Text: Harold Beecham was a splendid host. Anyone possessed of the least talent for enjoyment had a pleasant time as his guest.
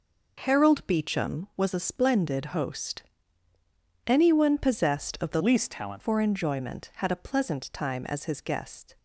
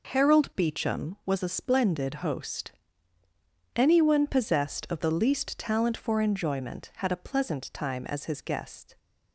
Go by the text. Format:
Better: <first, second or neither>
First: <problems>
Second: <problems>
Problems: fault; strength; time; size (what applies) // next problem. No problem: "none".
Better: second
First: changes voice from "least" to "talent"; from 5.3 to 6.0 s; 0.7 s long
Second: none